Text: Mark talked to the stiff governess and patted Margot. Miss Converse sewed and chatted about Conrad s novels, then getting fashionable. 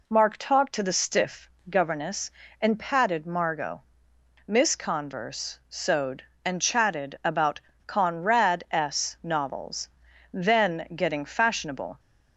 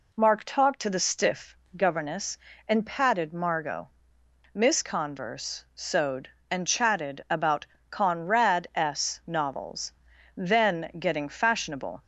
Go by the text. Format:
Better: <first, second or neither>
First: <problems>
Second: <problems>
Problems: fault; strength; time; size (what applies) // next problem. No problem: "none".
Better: neither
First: pauses between "stiff" and "governess"; slight; at 1.4 s; 0.18 s long // pauses between "about" and "Conrad"; slight; at 7.5 s; 0.28 s long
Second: pauses between "stiff" and "governess"; slight; at 1.5 s; 0.18 s long // pauses between "about" and "Conrad"; slight; at 7.6 s; 0.26 s long